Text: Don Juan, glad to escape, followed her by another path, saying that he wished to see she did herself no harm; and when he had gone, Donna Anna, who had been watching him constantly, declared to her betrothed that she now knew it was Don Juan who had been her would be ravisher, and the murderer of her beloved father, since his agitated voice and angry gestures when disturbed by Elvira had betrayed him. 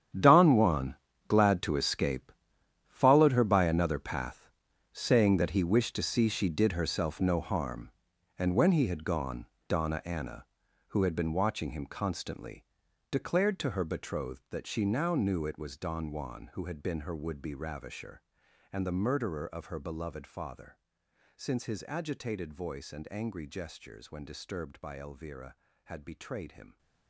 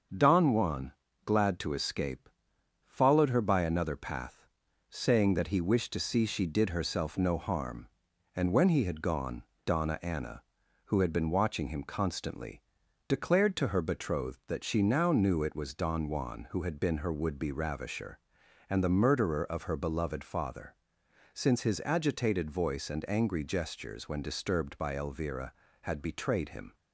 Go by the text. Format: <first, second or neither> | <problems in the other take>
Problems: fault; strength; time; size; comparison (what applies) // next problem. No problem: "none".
second | gets quieter; strong; throughout; 15.5 dB // starts louder than the rest; strong; until 1.5 s; 9.5 dB; also in the second